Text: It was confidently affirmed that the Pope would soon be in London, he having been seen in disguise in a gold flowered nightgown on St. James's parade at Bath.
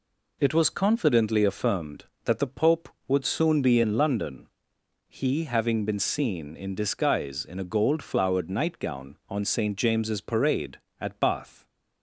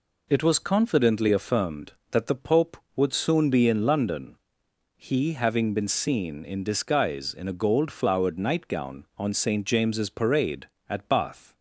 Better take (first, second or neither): neither